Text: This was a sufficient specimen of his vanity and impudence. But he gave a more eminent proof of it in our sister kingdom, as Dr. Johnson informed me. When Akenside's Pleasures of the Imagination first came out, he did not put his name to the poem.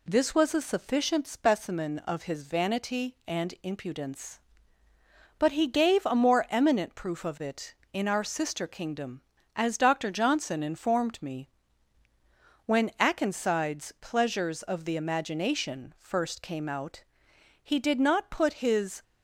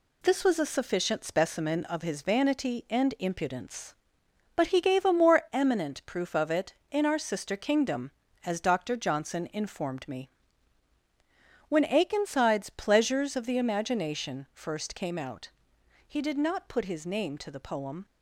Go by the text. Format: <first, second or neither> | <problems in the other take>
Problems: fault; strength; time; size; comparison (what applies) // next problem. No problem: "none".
second | stops before "name to the poem"; at 19.0 s